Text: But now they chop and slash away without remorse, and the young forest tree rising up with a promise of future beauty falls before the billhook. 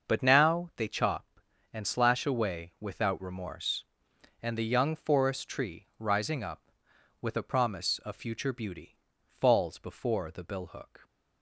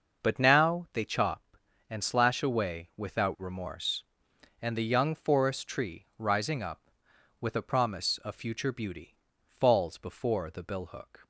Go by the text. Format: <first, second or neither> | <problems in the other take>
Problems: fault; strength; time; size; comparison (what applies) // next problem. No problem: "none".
neither | starts louder than the rest; the same in both // pauses between "beauty" and "falls"; slight; the same in both